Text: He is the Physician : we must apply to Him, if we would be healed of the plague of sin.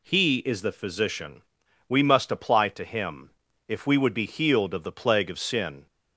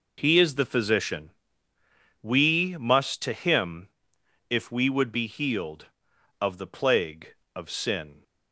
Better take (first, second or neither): first